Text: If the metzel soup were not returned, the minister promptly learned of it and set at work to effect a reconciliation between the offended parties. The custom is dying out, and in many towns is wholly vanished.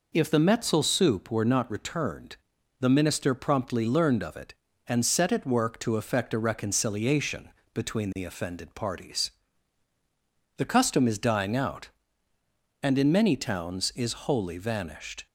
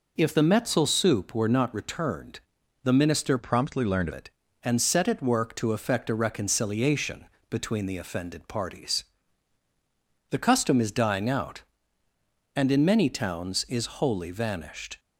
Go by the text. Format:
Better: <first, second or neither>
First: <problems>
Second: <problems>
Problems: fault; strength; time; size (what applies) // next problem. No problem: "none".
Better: first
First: pauses between "reconciliation" and "between"; slight; at 7.4 s; 0.24 s long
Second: changes voice from "promptly" to "of"; from 3.3 to 4.1 s; 0.8 s long // pauses between "reconciliation" and "between"; slight; at 7.2 s; 0.24 s long